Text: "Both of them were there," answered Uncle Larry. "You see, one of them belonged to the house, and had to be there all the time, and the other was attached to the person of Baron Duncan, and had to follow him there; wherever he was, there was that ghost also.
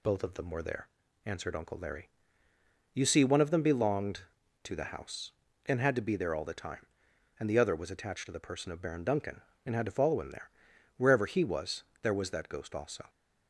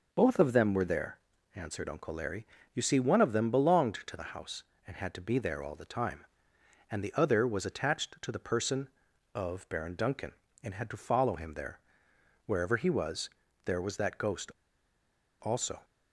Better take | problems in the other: first | pauses between "ghost" and "also"; noticeable; at 14.5 s; 0.88 s long

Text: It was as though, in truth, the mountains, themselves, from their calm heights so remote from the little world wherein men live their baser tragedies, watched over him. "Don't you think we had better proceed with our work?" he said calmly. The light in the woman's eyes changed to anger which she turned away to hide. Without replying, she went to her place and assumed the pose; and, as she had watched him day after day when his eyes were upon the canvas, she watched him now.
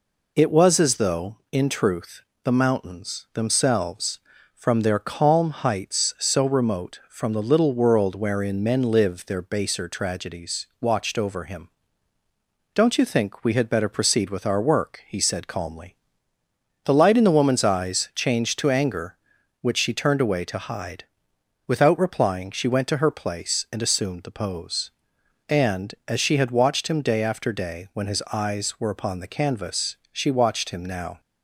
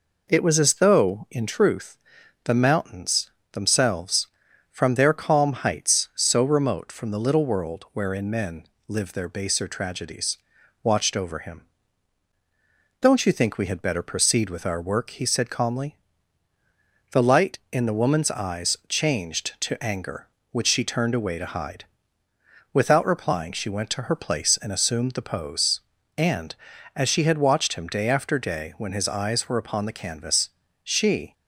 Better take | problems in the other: first | pauses between "men" and "live"; slight; at 8.6 s; 0.22 s long // stops before "watched him now"; at 31.3 s

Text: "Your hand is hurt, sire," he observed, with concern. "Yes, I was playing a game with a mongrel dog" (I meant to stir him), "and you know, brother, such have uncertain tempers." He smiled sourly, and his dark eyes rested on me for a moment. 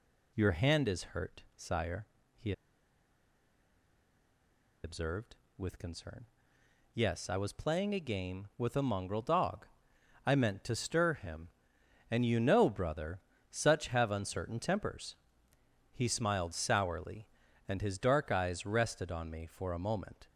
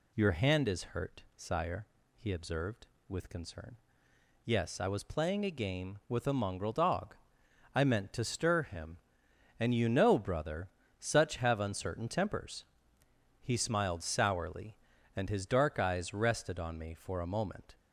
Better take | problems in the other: second | pauses between "he" and "observed"; strong; at 2.5 s; 2.3 s long

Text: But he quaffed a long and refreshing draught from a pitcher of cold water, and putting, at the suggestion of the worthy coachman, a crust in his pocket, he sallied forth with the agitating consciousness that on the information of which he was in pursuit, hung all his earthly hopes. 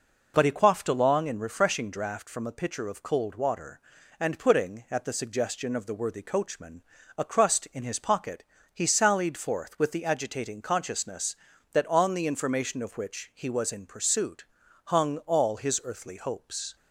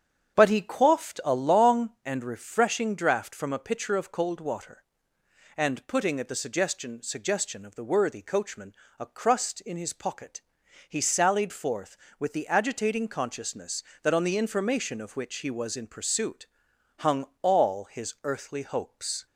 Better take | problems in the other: first | starts louder than the rest; strong; until 1.4 s; 8 dB // says "suggestion" twice; at 7.0 s // pauses between "hung" and "all"; slight; at 17.2 s; 0.18 s long

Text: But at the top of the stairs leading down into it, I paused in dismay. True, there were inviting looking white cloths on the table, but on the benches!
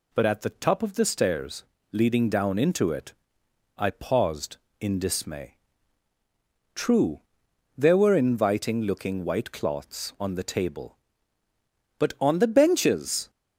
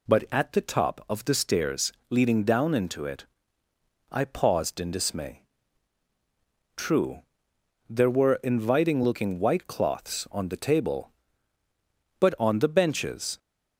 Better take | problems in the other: neither | pauses between "stairs" and "leading"; slight; the same in both

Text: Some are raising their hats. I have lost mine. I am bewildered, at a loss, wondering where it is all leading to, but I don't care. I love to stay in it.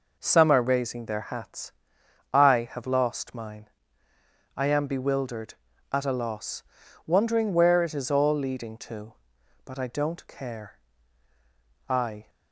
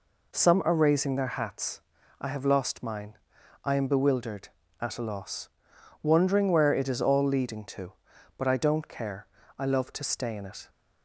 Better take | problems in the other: second | stops before "love to stay in it"; at 12.2 s

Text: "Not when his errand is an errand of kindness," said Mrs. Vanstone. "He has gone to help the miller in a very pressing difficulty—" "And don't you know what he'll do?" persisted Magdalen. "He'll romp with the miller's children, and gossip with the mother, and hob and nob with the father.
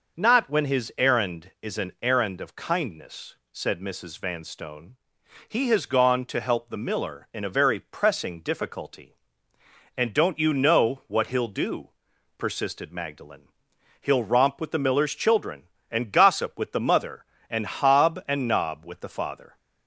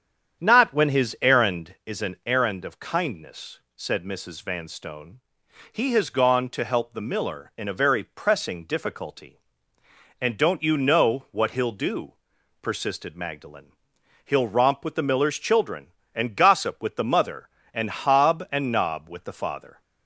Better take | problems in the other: first | starts louder than the rest; strong; until 1.8 s; 8.5 dB

